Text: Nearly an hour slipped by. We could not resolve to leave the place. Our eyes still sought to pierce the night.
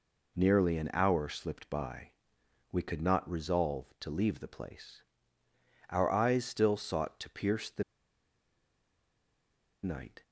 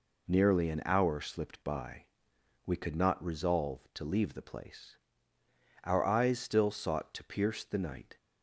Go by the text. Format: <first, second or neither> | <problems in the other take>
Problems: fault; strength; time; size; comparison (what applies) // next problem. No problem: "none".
second | pauses between "the" and "night"; strong; at 7.8 s; 2.0 s long